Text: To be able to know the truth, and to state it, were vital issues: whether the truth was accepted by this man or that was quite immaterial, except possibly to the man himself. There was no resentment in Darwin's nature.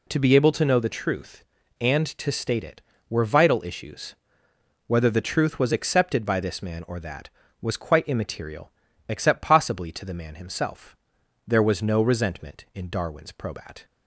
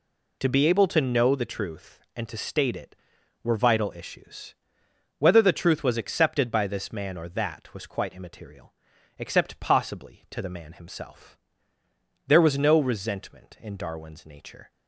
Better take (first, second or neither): second